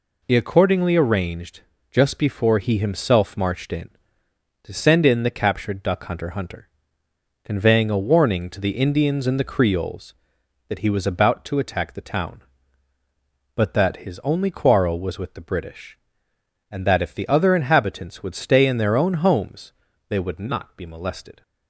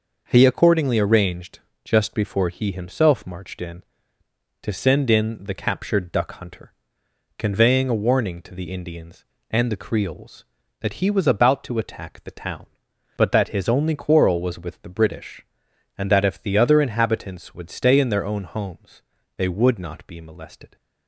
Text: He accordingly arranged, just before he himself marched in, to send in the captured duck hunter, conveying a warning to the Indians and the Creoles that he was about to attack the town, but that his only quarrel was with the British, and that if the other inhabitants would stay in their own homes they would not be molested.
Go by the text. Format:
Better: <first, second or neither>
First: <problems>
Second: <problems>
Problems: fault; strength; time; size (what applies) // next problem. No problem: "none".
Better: second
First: says "hunter" twice; at 6.3 s // pauses between "homes" and "they"; slight; at 19.7 s; 0.36 s long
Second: pauses between "homes" and "they"; slight; at 19.0 s; 0.34 s long